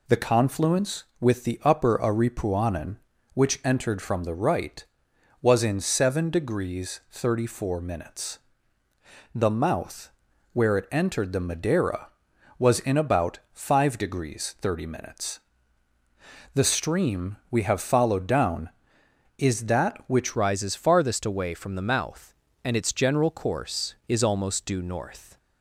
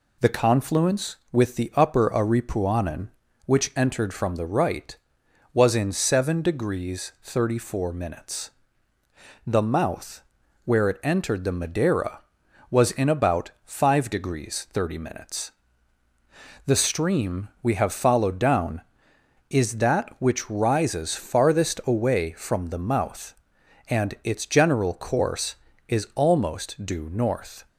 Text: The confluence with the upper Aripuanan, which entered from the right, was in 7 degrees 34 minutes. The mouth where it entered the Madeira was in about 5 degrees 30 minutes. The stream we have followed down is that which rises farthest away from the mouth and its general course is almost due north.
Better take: second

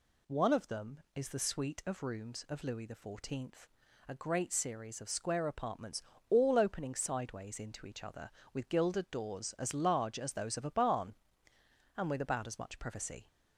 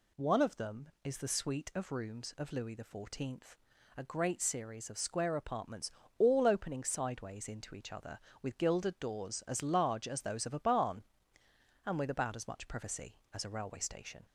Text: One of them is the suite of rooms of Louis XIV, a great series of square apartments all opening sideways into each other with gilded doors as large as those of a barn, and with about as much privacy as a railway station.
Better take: second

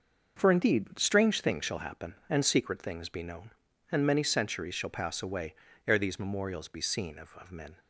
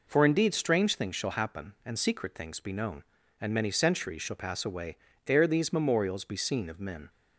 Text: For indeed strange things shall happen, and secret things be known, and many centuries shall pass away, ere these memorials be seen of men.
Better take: second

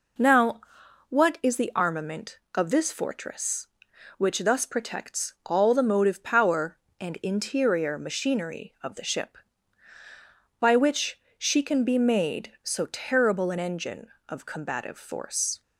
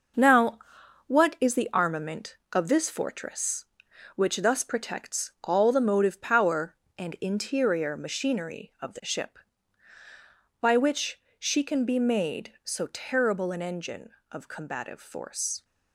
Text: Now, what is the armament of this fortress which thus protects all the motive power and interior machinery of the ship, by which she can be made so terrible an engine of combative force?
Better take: first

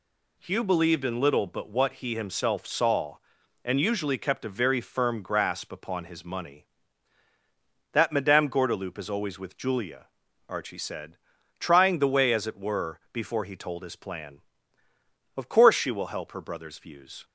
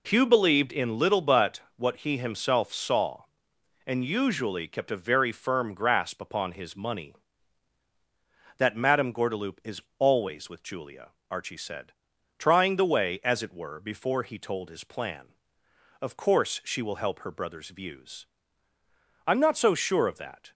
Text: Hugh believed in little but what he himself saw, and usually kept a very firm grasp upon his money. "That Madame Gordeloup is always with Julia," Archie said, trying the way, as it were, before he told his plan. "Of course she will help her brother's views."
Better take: first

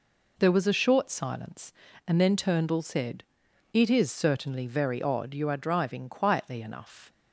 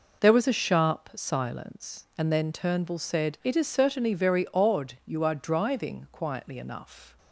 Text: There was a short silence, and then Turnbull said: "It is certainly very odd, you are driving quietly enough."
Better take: first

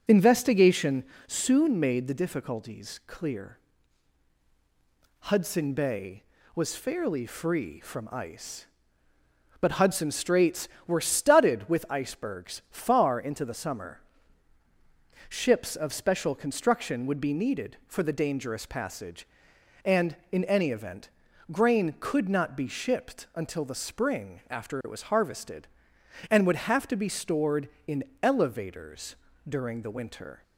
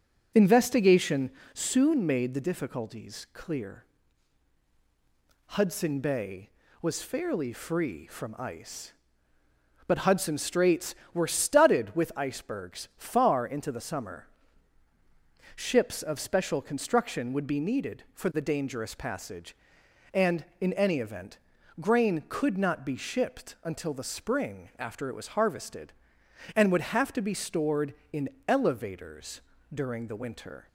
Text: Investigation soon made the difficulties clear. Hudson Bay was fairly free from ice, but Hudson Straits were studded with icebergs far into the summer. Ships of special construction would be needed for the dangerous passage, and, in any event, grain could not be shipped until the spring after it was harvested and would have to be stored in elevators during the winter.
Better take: neither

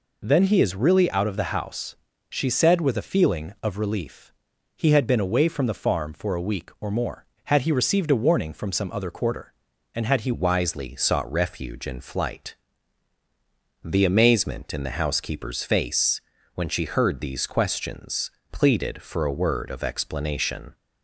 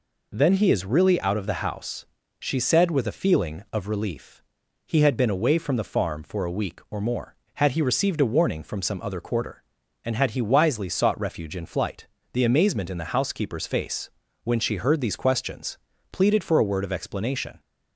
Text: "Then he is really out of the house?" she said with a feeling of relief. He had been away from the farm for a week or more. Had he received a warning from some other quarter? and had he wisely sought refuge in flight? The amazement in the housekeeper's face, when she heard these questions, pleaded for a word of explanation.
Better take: second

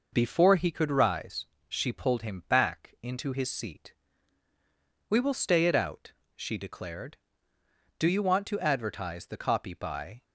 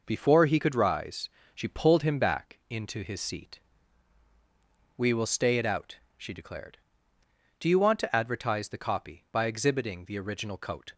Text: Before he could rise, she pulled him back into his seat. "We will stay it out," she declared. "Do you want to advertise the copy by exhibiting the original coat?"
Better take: second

